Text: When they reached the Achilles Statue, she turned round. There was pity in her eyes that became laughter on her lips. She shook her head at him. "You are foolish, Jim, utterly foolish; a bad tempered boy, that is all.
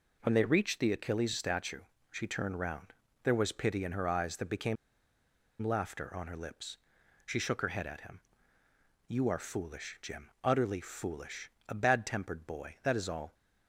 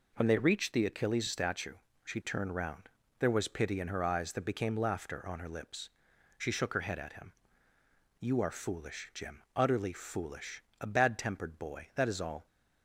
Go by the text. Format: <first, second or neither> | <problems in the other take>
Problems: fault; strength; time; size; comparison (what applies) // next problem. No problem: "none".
second | pauses between "became" and "laughter"; noticeable; at 4.7 s; 0.86 s long